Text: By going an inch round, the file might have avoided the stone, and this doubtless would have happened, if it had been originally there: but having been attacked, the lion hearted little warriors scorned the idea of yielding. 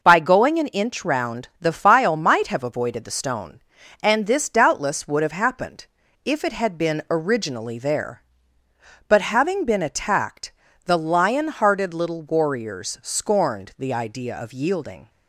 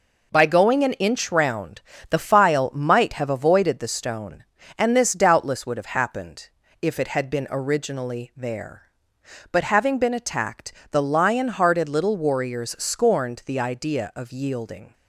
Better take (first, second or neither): neither